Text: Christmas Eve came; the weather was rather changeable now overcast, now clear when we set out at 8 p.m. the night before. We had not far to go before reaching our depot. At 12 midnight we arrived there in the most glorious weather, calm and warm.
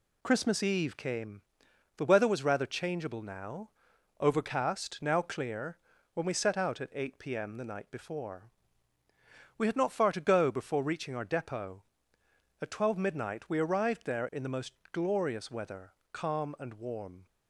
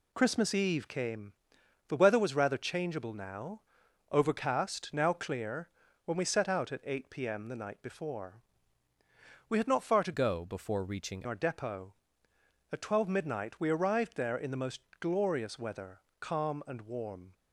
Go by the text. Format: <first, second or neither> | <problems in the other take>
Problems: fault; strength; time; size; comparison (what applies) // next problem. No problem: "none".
first | pauses between "now" and "overcast"; noticeable; at 3.6 s; 0.50 s long; noticeable in the first // pauses between "clear" and "when"; slight; at 5.6 s; 0.36 s long; slight in the first // changes voice from "go" to "reaching"; from 10.1 to 11.2 s; 1.1 s long // pauses between "most" and "glorious"; slight; at 14.8 s; 0.18 s long; slight in the first